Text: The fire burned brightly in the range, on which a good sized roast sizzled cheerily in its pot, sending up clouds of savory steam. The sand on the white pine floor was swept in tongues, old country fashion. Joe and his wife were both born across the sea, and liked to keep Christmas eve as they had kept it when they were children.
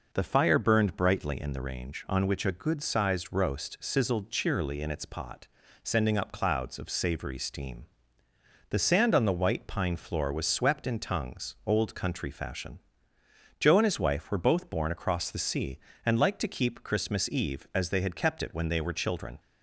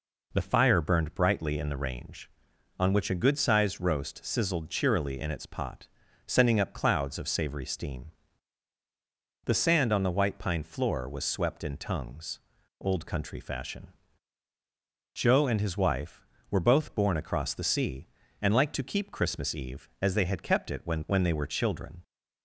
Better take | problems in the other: first | says "when" twice; at 21.0 s

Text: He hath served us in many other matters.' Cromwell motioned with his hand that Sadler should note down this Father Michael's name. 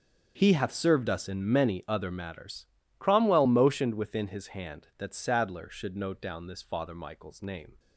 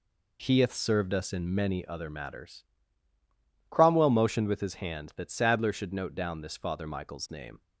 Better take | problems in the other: second | starts louder than the rest; until 1.3 s; 7 dB // says "within" for "with"; at 3.9 s

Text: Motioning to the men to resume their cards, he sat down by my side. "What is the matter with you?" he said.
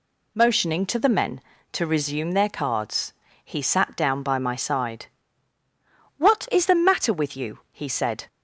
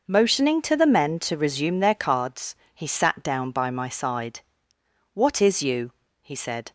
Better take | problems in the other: first | skips "the matter with"; at 5.6 s

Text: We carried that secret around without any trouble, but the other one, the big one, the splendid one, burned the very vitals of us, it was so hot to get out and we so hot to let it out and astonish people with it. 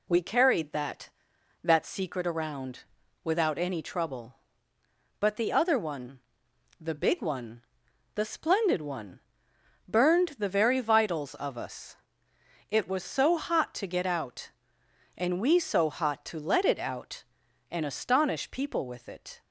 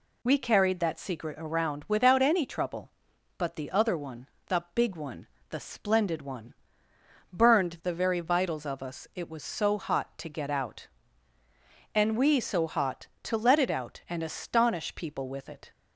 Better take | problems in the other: second | says "that" twice; at 1.6 s // pauses between "around" and "without"; at 2.8 s; 0.38 s long

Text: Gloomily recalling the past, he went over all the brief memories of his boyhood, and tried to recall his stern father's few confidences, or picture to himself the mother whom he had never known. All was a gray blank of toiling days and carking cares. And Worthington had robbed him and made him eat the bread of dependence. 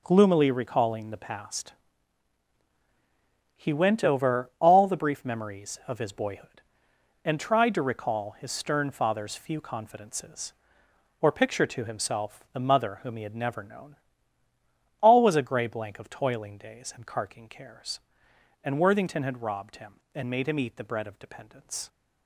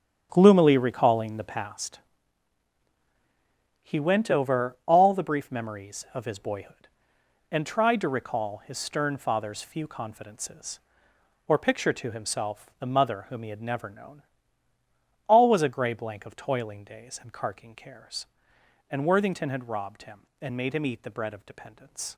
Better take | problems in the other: first | starts louder than the rest; strong; until 1.7 s; 8.5 dB

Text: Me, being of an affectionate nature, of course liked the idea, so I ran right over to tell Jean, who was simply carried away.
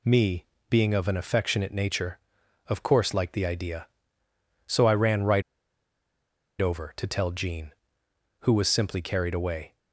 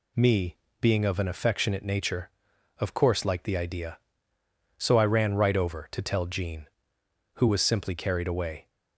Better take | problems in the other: second | pauses between "right" and "over"; at 5.4 s; 1.1 s long

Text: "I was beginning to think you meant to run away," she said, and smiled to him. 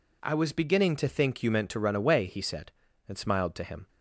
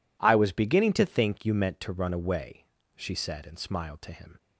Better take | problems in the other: second | says "he" for "she"; at 2.2 s

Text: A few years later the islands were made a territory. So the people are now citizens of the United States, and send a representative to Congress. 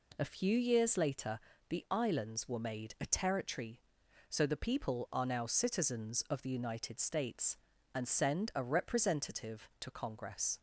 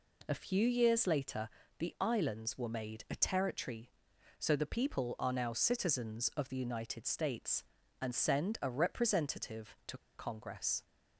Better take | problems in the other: first | pauses between "later" and "the"; slight; at 1.4 s; 0.32 s long; slight in the first // pauses between "to" and "Congress"; slight; at 9.9 s; 0.18 s long

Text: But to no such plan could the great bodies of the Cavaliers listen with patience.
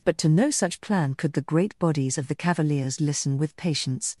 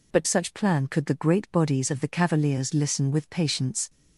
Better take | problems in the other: first | skips "to no"; at 0.2 s

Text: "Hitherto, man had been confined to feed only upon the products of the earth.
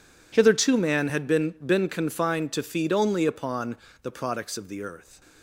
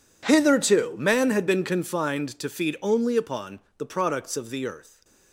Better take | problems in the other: second | says "been" twice; at 1.6 s // pauses between "upon" and "the"; slight; at 3.7 s; 0.26 s long; slight in the second

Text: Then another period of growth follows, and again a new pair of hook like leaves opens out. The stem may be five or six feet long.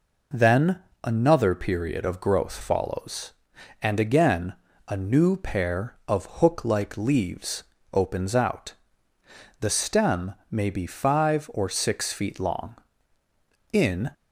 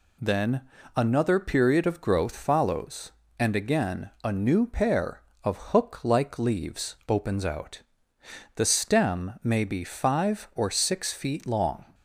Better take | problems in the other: second | pauses between "Then" and "another"; slight; at 0.7 s; 0.26 s long; slight in the second // pauses between "again" and "a"; slight; at 4.5 s; 0.34 s long // pauses between "leaves" and "opens"; slight; at 7.6 s; 0.28 s long // pauses between "stem" and "may"; slight; at 10.3 s; 0.16 s long // goes on to say "In"; slight; from 13.7 s on; 0.38 s long

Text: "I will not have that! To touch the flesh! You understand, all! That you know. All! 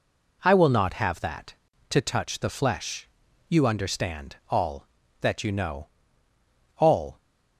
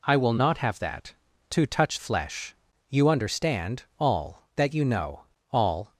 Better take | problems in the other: first | skips "the"; at 1.9 s

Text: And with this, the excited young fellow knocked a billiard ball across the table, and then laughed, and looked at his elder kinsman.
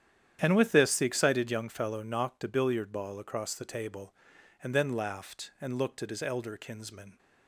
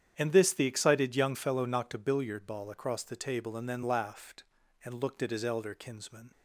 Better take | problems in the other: first | starts louder than the rest; strong; until 1.1 s; 9 dB; strong in the first // skips "with"; at 0.3 s

